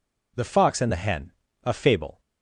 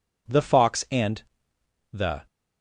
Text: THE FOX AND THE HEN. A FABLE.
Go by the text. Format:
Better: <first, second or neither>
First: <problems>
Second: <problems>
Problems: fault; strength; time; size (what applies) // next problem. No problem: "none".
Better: first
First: none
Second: pauses between "AND" and "THE"; noticeable; at 1.2 s; 0.70 s long // stops before "HEN A FABLE"; at 2.2 s